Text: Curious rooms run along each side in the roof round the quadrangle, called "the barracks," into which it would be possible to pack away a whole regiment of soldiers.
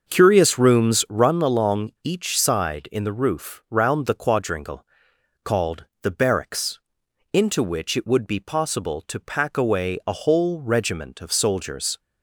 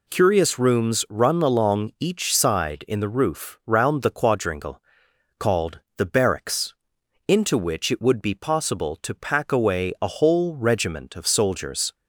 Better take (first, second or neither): second